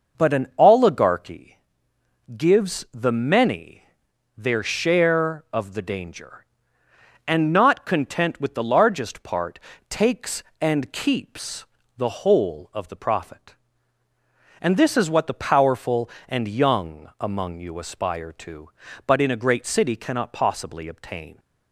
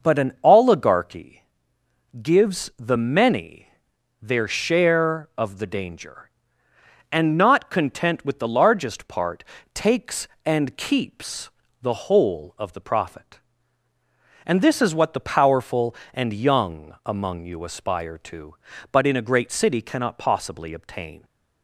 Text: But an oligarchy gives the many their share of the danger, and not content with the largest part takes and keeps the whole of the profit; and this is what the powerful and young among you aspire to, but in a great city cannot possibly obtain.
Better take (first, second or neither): neither